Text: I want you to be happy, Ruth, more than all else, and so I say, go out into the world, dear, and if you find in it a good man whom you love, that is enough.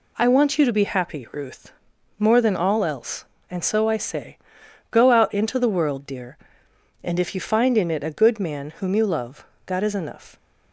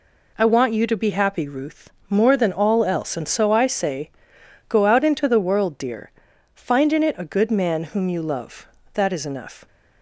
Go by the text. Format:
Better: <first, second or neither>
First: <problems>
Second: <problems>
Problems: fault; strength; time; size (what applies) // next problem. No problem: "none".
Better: first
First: none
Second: skips "and if you"; at 6.3 s